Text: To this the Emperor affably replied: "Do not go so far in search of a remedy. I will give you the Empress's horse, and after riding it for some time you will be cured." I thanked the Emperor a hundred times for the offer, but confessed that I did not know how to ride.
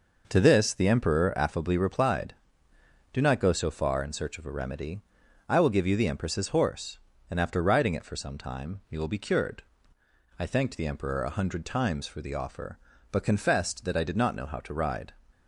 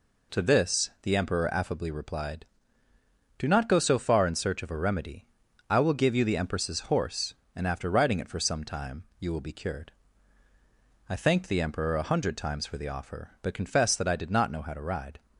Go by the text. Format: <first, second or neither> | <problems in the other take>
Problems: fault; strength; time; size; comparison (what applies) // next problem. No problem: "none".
neither | none